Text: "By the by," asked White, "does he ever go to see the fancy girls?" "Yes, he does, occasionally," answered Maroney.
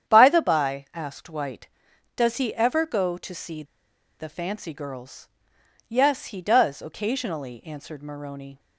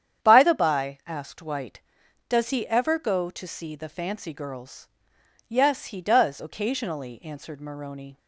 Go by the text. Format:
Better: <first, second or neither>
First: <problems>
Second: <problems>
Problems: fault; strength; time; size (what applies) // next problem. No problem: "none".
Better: second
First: starts louder than the rest; strong; until 1.1 s; 9 dB // pauses between "see" and "the"; noticeable; at 3.6 s; 0.55 s long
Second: starts louder than the rest; strong; until 1.3 s; 9 dB